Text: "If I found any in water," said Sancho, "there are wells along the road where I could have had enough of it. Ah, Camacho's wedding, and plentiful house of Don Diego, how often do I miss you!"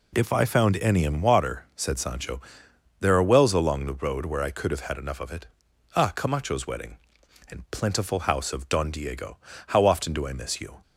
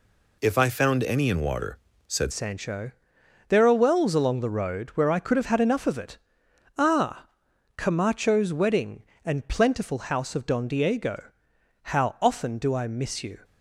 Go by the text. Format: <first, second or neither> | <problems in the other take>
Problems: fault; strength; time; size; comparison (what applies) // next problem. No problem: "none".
first | changes voice at "Sancho"; from 2.3 s on; 11.1 s long